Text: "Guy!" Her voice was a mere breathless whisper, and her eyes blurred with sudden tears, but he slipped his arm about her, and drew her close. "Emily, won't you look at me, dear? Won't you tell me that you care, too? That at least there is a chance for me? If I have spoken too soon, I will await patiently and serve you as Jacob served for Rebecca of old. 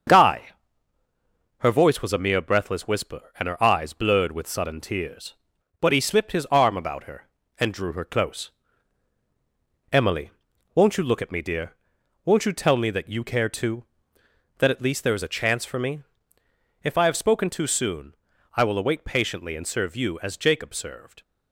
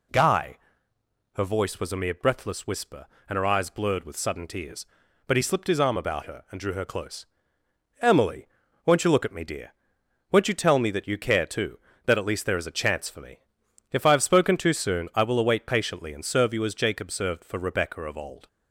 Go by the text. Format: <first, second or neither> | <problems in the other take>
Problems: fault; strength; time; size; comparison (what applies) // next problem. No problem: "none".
second | starts louder than the rest; until 2.1 s; 7 dB // stops before "for Rebecca of old"; at 21.2 s